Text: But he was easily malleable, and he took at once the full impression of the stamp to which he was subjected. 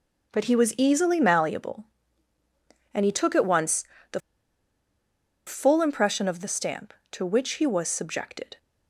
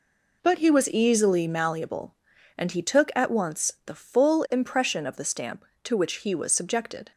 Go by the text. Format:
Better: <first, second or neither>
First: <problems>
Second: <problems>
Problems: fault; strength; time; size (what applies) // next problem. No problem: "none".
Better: second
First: pauses between "once" and "the"; slight; at 3.8 s; 0.28 s long // pauses between "the" and "full"; strong; at 4.1 s; 1.2 s long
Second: none